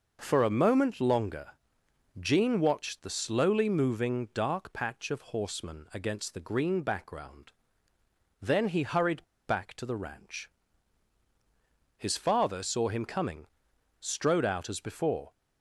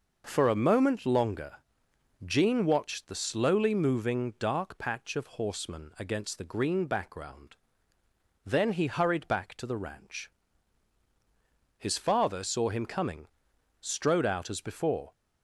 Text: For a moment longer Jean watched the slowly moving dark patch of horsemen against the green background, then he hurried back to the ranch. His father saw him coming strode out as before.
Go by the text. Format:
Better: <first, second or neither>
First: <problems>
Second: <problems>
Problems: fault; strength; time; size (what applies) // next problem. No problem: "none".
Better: second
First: pauses between "longer" and "Jean"; noticeable; at 1.5 s; 0.68 s long // pauses between "hurried" and "back"; slight; at 9.2 s; 0.23 s long // pauses between "coming" and "strode"; noticeable; at 13.4 s; 0.54 s long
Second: pauses between "longer" and "Jean"; noticeable; at 1.5 s; 0.68 s long // pauses between "coming" and "strode"; noticeable; at 13.2 s; 0.54 s long